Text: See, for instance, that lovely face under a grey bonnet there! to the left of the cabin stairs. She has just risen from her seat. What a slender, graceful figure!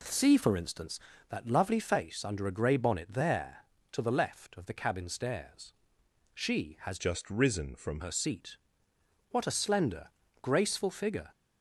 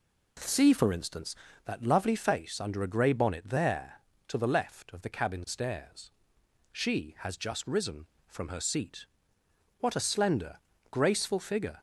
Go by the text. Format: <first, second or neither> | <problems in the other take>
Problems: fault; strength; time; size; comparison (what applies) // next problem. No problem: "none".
second | changes voice from "just" to "from"; from 6.9 to 7.9 s; 1.0 s long